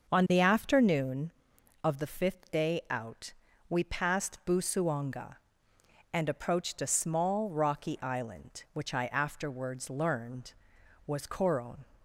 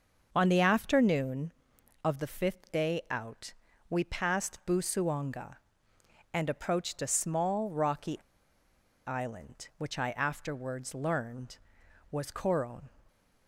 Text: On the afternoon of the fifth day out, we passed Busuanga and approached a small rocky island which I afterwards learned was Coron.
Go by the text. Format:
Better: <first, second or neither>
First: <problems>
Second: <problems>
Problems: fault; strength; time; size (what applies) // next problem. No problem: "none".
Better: first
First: starts louder than the rest; until 1.1 s; 6.5 dB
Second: starts louder than the rest; until 1.3 s; 6.5 dB // pauses between "rocky" and "island"; noticeable; at 8.1 s; 0.88 s long